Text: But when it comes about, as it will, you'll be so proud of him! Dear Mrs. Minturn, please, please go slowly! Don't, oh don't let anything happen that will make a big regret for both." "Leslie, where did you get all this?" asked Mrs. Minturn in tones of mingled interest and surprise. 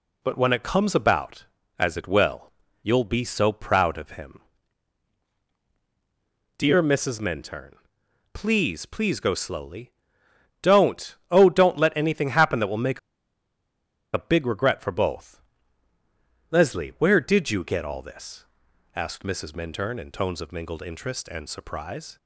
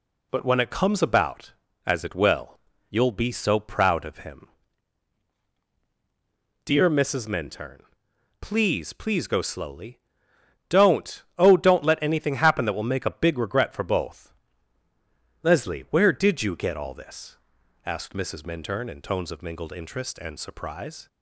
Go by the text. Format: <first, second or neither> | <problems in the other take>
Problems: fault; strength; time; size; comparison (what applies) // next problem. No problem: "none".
second | pauses between "make" and "a"; at 12.9 s; 1.1 s long